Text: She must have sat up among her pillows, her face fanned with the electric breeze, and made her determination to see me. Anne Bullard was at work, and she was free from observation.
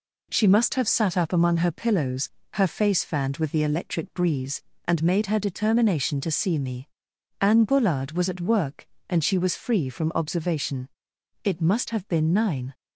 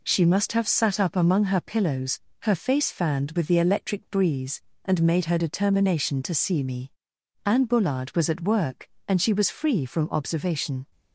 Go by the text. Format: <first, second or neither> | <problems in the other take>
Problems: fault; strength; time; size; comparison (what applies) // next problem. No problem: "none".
second | goes on to say "It must have been nine"; noticeable; from 11.4 s on; 1.3 s long